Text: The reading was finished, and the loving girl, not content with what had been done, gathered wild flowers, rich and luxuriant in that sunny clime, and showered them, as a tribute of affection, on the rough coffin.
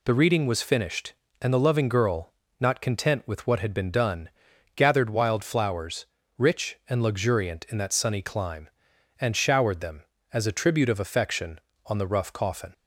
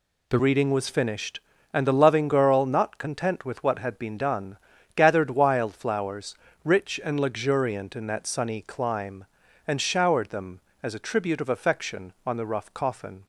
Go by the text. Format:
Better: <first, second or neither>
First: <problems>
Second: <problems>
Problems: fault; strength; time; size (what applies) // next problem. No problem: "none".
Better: first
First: none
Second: changes voice at "reading"; from 0.3 s on; 12.9 s long